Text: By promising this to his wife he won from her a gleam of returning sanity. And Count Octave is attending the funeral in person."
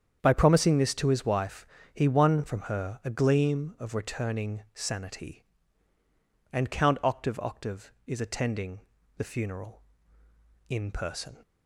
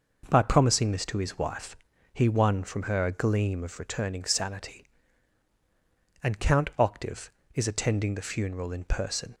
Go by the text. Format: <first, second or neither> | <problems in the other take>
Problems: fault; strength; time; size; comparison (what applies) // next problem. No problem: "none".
second | starts louder than the rest; strong; until 1.2 s; 8 dB // pauses between "wife" and "he"; slight; at 1.6 s; 0.28 s long; also in the second // says "Octave" twice; at 7.3 s // pauses between "attending" and "the"; at 8.7 s; 0.38 s long